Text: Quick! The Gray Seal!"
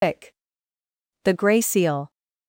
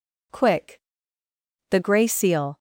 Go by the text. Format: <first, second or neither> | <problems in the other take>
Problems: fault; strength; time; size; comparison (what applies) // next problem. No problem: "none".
second | loses the start of "Quick"; at 0.0 s; 170 ms